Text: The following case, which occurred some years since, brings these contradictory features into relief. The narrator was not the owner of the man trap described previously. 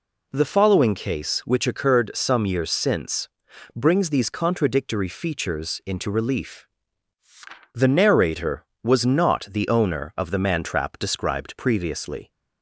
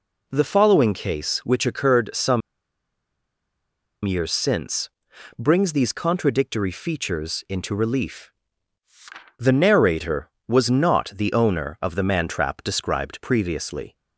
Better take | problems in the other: first | pauses between "some" and "years"; strong; at 2.4 s; 1.6 s long

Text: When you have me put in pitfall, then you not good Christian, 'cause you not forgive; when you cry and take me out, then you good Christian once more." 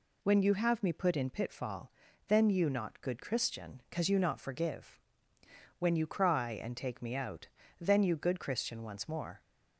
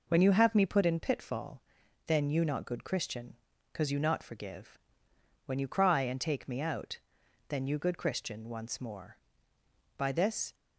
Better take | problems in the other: first | goes on to say "By this"; from 9.9 s on; 0.56 s long

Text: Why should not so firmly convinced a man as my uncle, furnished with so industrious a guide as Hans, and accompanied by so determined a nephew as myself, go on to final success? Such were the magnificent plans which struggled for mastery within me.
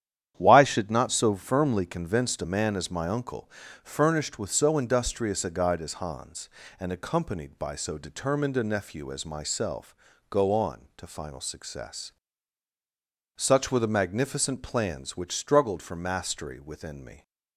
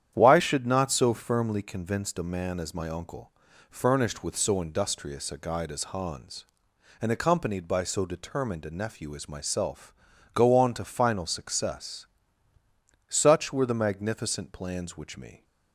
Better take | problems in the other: first | starts louder than the rest; strong; until 1.1 s; 9.5 dB; strong in the first // skips "struggled for mastery within"; at 15.1 s

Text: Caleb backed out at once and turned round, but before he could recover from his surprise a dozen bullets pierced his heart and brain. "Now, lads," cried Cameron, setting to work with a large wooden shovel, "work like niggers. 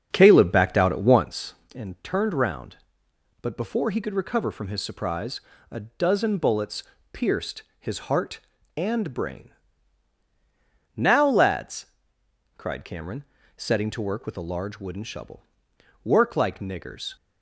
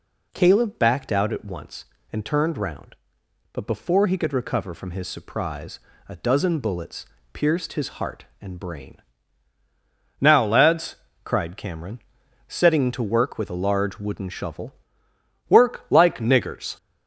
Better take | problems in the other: second | starts louder than the rest; until 1.3 s; 6.5 dB // pauses between "surprise" and "a"; slight; at 5.3 s; 0.30 s long; slight in the second // pauses between "bullets" and "pierced"; slight; at 6.8 s; 0.28 s long; slight in the second // pauses between "pierced" and "his"; slight; at 7.6 s; 0.18 s long

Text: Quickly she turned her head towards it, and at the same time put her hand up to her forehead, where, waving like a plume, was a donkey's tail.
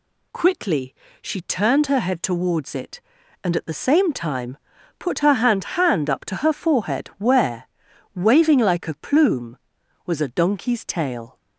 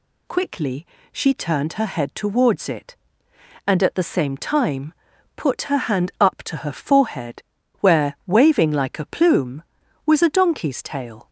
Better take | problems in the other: second | pauses between "Quickly" and "she"; slight; at 0.9 s; 0.28 s long; slight in the second // pauses between "time" and "put"; at 4.5 s; 0.40 s long; also in the second // says "hand" twice; at 5.8 s

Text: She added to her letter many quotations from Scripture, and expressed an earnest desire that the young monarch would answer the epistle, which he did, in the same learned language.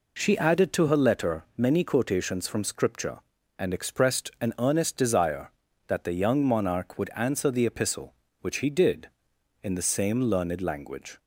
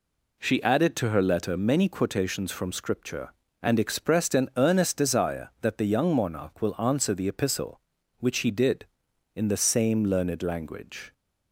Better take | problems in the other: first | says "will" for "would"; at 6.6 s

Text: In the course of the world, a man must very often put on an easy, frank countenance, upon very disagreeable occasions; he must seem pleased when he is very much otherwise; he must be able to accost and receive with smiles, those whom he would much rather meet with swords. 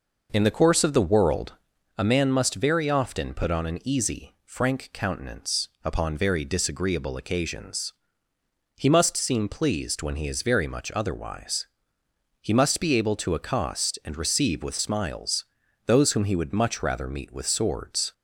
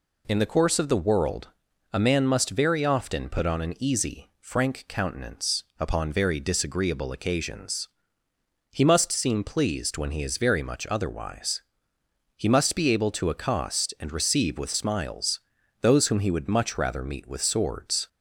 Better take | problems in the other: second | starts louder than the rest; noticeable; until 1.9 s; 5.5 dB

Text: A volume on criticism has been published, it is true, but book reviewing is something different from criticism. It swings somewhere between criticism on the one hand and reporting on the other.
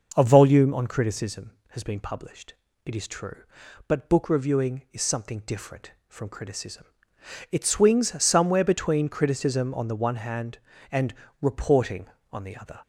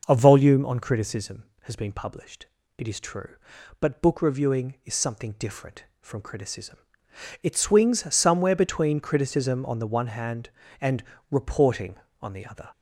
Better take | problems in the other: neither | pauses between "and" and "reporting"; slight; the same in both

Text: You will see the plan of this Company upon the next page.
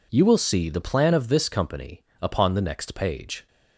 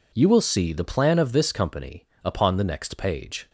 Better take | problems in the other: neither | pauses between "Company" and "upon"; slight; the same in both

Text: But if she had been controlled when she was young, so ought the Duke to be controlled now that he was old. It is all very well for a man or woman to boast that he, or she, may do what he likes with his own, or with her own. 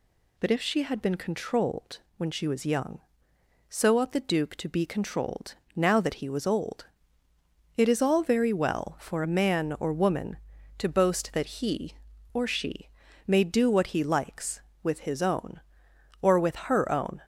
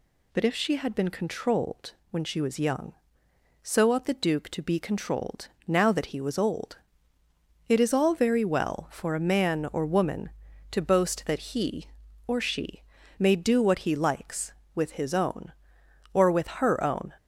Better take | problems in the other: neither | pauses between "controlled" and "when"; slight; the same in both // pauses between "controlled" and "now"; slight; the same in both

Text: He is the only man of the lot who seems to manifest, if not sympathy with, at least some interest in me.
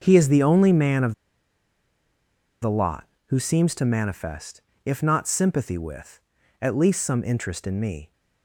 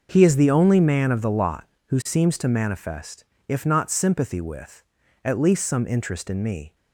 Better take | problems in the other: second | pauses between "of" and "the"; strong; at 1.1 s; 1.4 s long

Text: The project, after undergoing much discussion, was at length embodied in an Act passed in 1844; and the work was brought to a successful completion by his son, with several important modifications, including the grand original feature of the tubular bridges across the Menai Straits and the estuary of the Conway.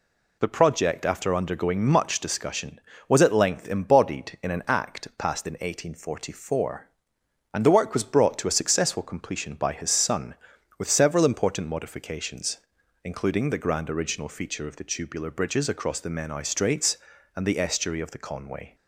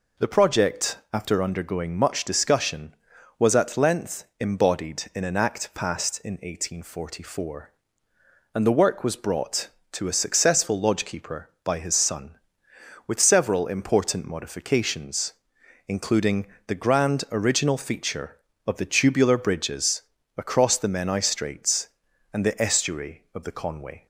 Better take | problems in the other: first | pauses between "length" and "embodied"; slight; at 4.2 s; 0.16 s long // says "lodgekeeper" for "completion"; at 10.7 s // pauses between "including" and "the"; slight; at 16.4 s; 0.20 s long // pauses between "bridges" and "across"; slight; at 20.0 s; 0.36 s long

